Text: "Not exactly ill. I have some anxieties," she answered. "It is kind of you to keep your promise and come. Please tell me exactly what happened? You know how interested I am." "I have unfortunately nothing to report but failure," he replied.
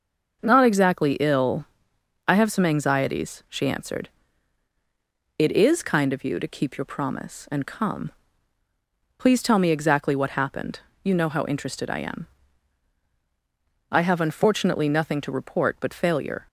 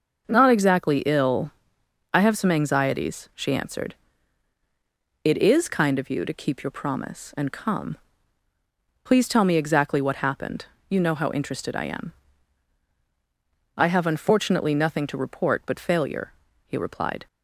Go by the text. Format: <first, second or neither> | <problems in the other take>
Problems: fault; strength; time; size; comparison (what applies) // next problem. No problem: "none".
second | starts louder than the rest; noticeable; until 1.4 s; 6 dB; noticeable in the second // stops before "he replied"; at 16.4 s